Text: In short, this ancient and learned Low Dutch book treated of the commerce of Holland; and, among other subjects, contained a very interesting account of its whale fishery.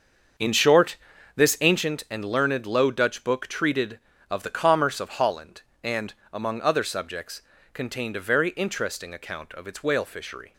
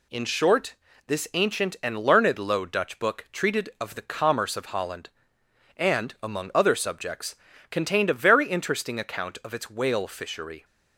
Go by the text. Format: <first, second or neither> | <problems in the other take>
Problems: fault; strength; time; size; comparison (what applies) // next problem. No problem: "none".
second | starts louder than the rest; until 1.9 s; 6.5 dB